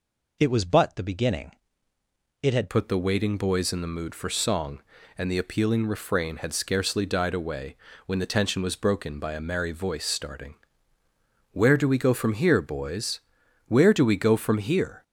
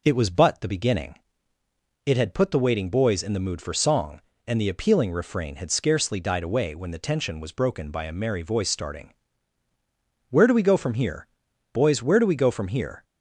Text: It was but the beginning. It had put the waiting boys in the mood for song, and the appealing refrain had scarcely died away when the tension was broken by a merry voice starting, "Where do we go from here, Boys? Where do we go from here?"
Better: second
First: changes voice at "put"; from 2.6 s on; 12.4 s long // pauses between "away" and "when"; slight; at 7.7 s; 0.32 s long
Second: none

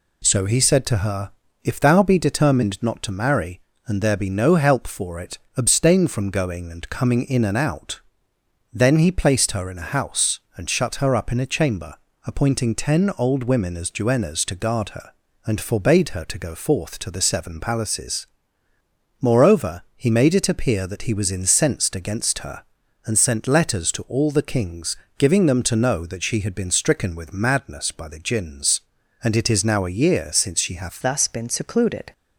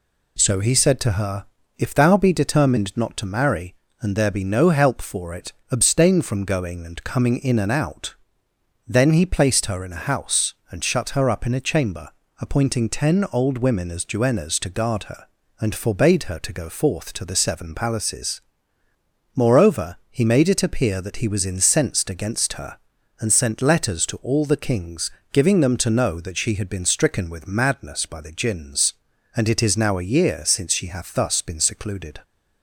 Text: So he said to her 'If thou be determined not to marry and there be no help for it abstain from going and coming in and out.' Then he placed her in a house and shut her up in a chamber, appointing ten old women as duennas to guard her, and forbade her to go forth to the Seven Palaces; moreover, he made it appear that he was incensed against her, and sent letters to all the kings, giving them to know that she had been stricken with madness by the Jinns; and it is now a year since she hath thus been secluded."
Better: second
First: pauses between "her" and "If"; slight; at 1.3 s; 0.32 s long // pauses between "it" and "abstain"; slight; at 5.3 s; 0.20 s long // changes voice at "thus"; from 31.0 s on; 1.1 s long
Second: pauses between "her" and "If"; slight; at 1.4 s; 0.32 s long // pauses between "it" and "abstain"; slight; at 5.5 s; 0.20 s long

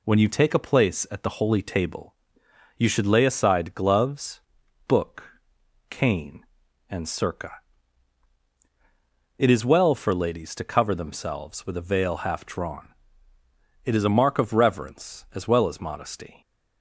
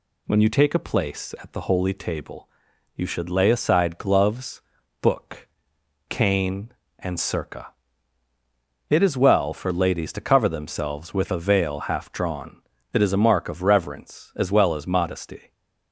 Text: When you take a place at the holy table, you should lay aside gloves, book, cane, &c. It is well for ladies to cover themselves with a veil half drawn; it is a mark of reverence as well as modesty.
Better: neither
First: none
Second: none

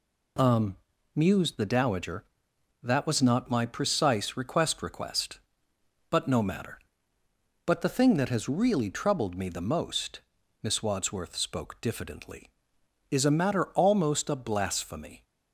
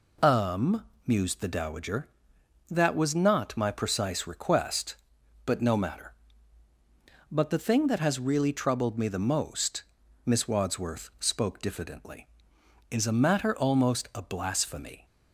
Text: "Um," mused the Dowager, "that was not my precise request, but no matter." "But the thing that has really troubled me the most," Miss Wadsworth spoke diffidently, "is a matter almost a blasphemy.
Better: second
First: says "request" twice; at 4.8 s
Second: none

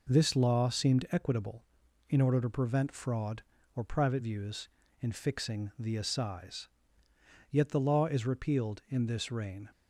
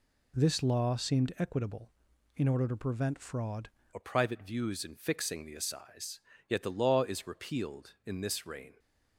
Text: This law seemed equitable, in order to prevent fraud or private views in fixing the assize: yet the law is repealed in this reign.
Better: first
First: none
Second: changes voice at "or"; from 3.9 s on; 4.8 s long

